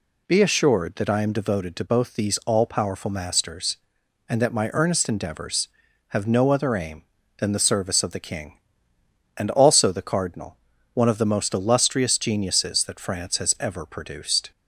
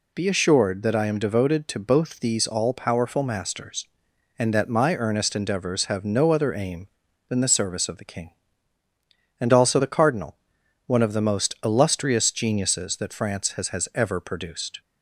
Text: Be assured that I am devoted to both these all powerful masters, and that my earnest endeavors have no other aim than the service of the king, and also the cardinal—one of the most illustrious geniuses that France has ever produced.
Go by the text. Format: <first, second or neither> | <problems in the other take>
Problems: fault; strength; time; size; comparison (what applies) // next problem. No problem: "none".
first | says "has" twice; at 13.6 s